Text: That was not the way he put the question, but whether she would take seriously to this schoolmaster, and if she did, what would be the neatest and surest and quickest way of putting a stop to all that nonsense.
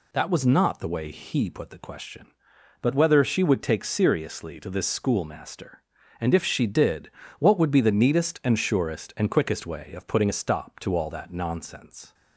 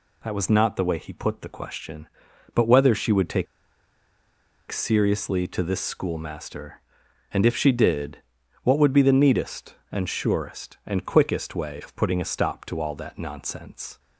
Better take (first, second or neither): first